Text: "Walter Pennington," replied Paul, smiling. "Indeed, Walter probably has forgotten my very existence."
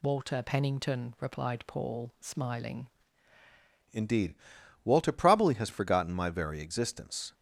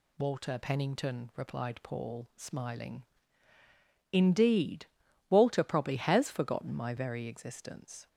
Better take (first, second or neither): second